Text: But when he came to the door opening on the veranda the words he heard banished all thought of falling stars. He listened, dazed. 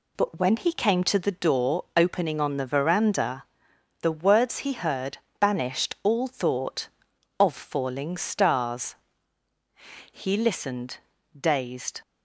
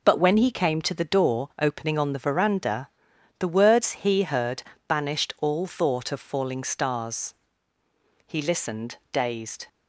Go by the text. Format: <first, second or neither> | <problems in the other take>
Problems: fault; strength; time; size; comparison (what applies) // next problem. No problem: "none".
neither | pauses between "veranda" and "the"; noticeable; the same in both // pauses between "heard" and "banished"; slight; the same in both